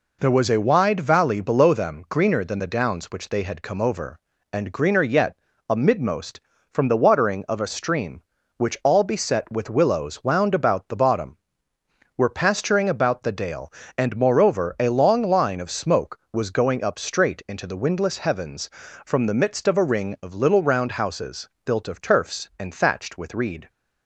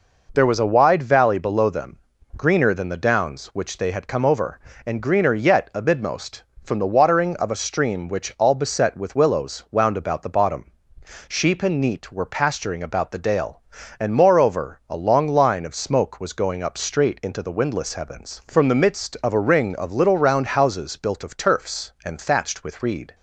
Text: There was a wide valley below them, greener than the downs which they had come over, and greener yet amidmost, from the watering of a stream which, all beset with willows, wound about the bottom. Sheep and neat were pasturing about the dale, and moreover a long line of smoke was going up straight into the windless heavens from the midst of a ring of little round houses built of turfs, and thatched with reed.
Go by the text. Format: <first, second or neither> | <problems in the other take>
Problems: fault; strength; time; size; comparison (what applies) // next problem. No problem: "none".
second | pauses between "yet" and "amidmost"; slight; at 5.3 s; 0.32 s long // skips "Sheep and neat"; at 11.7 s // pauses between "houses" and "built"; slight; at 21.4 s; 0.16 s long